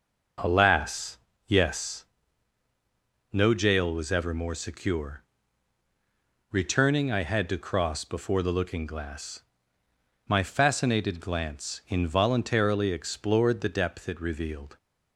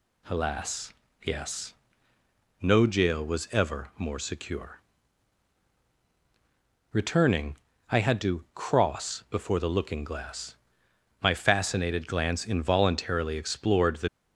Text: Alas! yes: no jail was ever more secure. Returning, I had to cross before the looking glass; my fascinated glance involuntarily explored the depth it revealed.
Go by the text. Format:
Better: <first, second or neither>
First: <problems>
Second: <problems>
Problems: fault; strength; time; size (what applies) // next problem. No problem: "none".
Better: first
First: none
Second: stops before "depth it revealed"; at 14.0 s